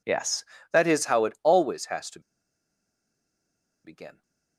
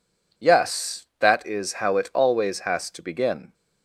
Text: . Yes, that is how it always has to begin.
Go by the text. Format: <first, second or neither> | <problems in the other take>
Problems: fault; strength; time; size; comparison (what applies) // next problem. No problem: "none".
second | pauses between "to" and "begin"; strong; at 2.1 s; 1.6 s long